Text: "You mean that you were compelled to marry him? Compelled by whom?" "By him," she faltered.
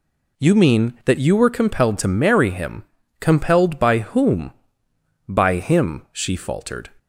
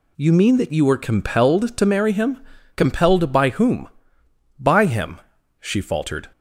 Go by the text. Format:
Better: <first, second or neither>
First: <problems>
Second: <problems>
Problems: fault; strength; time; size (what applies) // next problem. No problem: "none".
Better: neither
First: none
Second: none